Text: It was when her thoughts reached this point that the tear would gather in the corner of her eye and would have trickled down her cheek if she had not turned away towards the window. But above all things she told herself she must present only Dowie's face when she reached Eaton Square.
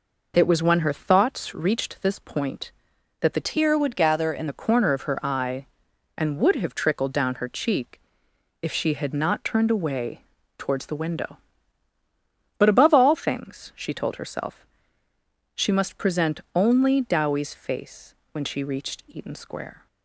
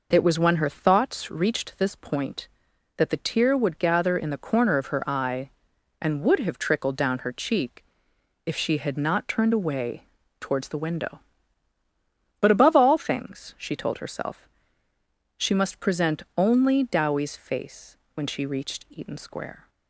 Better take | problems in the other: second | changes voice from "tear" to "in"; from 3.4 to 4.4 s; 1.0 s long // pauses between "cheek" and "if"; noticeable; at 8.0 s; 0.60 s long; noticeable in the second // pauses between "away" and "towards"; slight; at 10.2 s; 0.32 s long; slight in the second // pauses between "herself" and "she"; noticeable; at 14.6 s; 0.90 s long; noticeable in the second // pauses between "face" and "when"; slight; at 18.1 s; 0.20 s long; slight in the second

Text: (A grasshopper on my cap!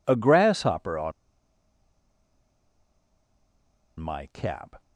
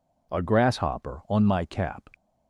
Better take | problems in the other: second | pauses between "on" and "my"; strong; at 1.1 s; 2.8 s long

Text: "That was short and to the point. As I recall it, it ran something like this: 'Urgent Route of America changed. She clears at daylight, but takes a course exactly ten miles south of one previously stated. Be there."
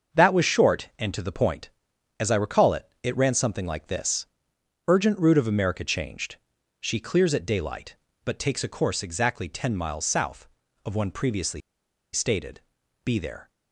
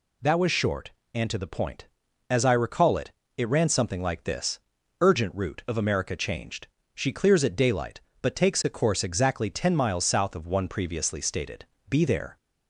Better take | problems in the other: second | starts louder than the rest; until 1.2 s; 6.5 dB // pauses between "previously" and "stated"; noticeable; at 11.6 s; 0.53 s long

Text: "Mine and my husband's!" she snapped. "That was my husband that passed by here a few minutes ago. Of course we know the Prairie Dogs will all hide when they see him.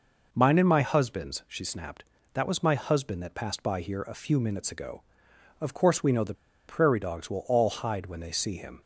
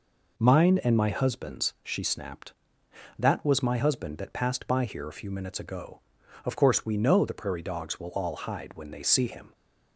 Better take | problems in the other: second | pauses between "the" and "Prairie"; slight; at 6.3 s; 0.35 s long

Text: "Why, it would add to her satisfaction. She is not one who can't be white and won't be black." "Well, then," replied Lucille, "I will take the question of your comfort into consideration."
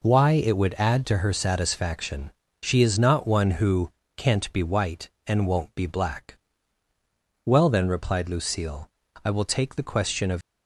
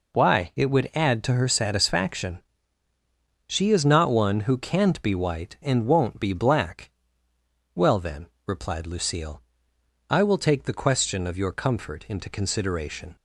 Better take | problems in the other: second | pauses between "who" and "can't"; slight; at 3.9 s; 0.24 s long // stops before "your comfort into consideration"; at 10.4 s

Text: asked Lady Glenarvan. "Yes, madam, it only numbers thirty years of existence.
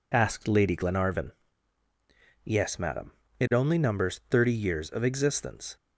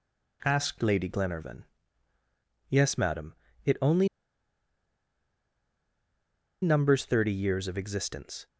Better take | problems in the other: first | pauses between "only" and "numbers"; strong; at 4.0 s; 2.5 s long

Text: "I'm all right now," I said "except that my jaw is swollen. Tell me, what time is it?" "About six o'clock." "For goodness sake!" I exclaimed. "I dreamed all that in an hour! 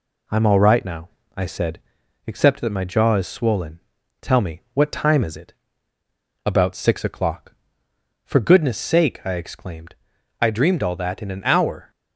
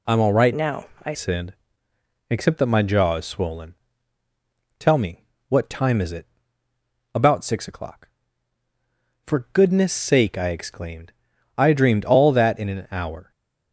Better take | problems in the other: first | changes voice from "now" to "I"; from 0.5 to 1.1 s; 0.6 s long // pauses between "said" and "except"; noticeable; at 1.5 s; 0.74 s long; noticeable in the first

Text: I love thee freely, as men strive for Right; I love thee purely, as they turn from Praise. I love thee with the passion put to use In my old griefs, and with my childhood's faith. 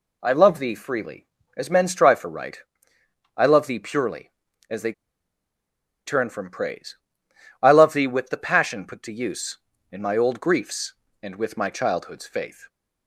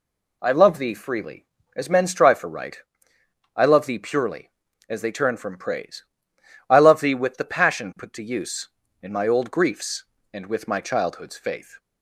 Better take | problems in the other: second | pauses between "they" and "turn"; at 4.9 s; 1.1 s long

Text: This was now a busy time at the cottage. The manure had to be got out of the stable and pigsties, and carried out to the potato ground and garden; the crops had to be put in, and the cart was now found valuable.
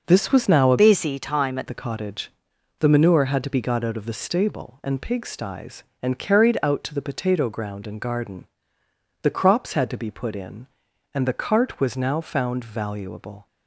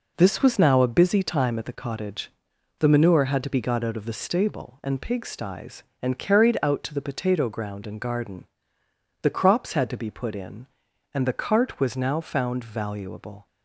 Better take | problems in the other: second | changes voice from "busy" to "at"; from 0.7 to 1.6 s; 0.9 s long

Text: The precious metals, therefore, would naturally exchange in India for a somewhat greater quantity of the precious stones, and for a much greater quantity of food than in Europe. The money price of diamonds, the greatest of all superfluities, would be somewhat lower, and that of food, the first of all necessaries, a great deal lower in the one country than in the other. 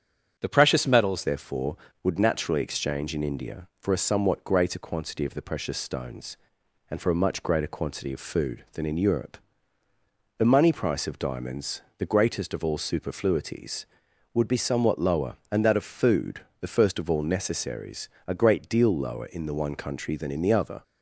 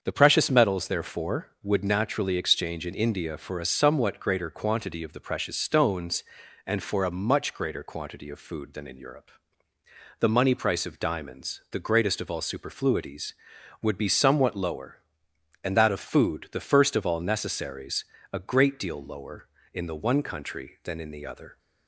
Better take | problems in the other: second | starts louder than the rest; strong; until 1.3 s; 8.5 dB; also in the second // changes voice at "therefore"; from 1.2 s on; 19.6 s long

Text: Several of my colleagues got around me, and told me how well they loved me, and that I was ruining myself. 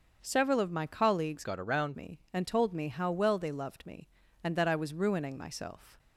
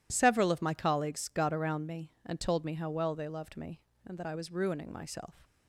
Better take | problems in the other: second | starts louder than the rest; until 1.2 s; 6.5 dB // changes voice from "got" to "around"; from 1.4 to 1.9 s; 0.5 s long

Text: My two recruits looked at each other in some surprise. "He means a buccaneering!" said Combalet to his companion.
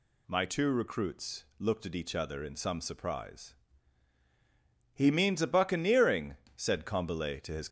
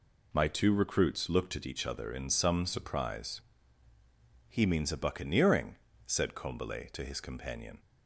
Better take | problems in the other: second | stops before "companion"; at 7.6 s

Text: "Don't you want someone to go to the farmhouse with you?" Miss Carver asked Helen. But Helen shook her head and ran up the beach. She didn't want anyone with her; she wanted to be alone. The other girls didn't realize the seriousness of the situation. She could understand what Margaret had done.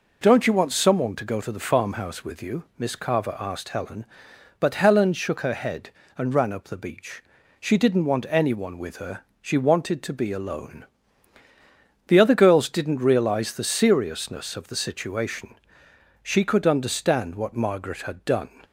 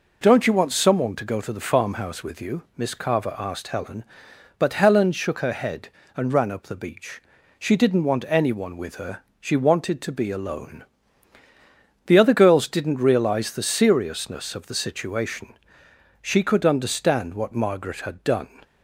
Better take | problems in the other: neither | none

